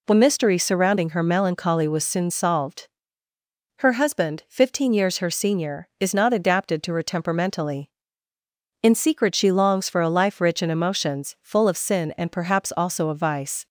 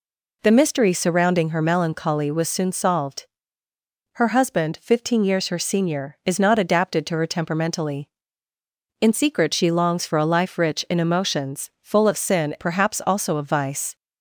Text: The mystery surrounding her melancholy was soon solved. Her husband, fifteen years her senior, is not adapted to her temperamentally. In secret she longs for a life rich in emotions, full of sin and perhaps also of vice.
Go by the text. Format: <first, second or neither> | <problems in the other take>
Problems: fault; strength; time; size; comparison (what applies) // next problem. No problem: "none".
first | skips "and"; at 12.5 s